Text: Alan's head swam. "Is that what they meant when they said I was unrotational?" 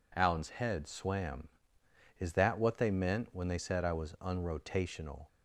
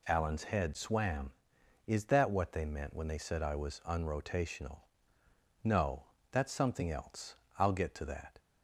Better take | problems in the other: first | goes on to say "No that's something else I'll get to that"; strong; from 5.6 s on; 2.7 s long

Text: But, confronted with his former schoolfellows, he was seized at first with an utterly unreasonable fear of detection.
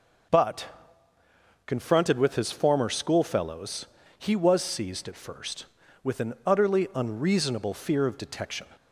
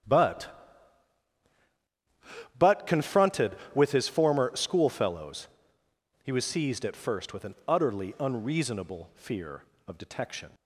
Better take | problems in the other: first | starts louder than the rest; strong; until 3.1 s; 9.5 dB; noticeable in the first // says "But" twice; at 2.5 s

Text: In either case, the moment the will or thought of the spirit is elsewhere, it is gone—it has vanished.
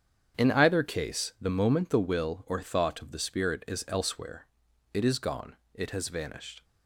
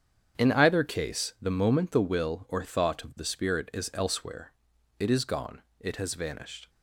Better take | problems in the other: neither | starts louder than the rest; strong; the same in both

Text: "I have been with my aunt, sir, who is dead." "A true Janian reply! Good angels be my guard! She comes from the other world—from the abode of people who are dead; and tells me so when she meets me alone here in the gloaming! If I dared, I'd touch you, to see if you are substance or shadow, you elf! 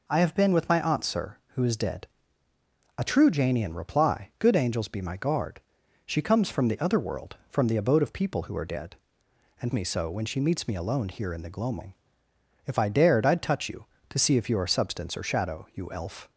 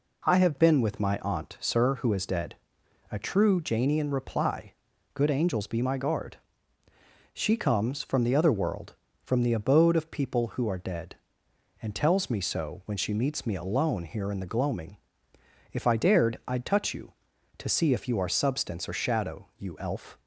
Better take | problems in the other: second | skips "tells"; at 9.7 s

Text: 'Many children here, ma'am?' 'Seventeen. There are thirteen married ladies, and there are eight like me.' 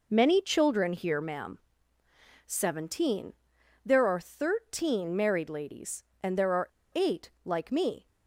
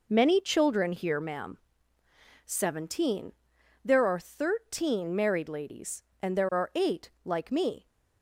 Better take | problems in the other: second | pauses between "are" and "eight"; slight; at 6.7 s; 0.24 s long

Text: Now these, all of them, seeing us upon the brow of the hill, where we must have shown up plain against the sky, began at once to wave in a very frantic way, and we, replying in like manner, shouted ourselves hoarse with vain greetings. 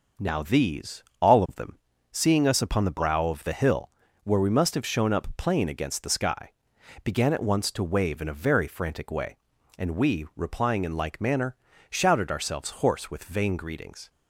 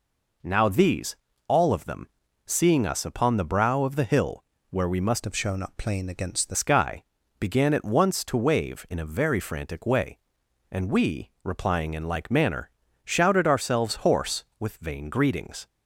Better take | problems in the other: first | changes voice from "have" to "the"; from 5.2 to 6.5 s; 1.3 s long

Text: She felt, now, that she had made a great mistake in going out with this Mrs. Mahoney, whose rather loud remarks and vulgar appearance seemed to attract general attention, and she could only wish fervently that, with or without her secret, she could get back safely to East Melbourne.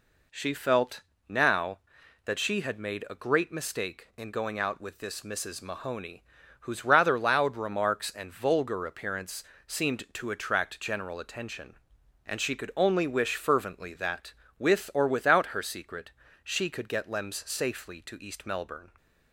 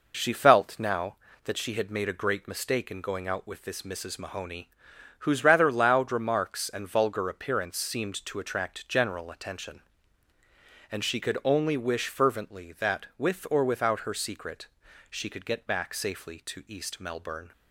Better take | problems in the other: second | pauses between "appearance" and "seemed"; slight; at 9.4 s; 0.22 s long // says "lems" for "back"; at 17.0 s

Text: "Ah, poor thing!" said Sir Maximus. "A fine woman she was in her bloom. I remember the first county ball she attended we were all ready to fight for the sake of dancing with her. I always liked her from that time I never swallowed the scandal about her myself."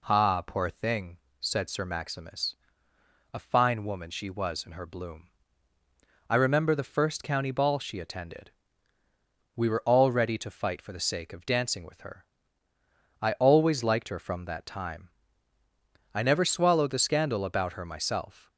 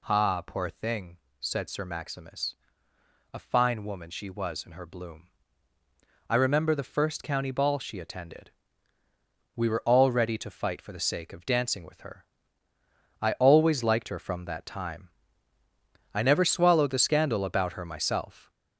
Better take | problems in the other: first | gets louder; noticeable; throughout; 6 dB // pauses between "attended" and "we"; at 8.5 s; 1.0 s long; also in the first // pauses between "time" and "I"; at 15.0 s; 1.0 s long; also in the first

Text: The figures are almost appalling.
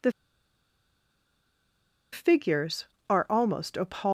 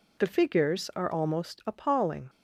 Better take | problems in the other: second | pauses between "The" and "figures"; strong; at 0.1 s; 2.0 s long

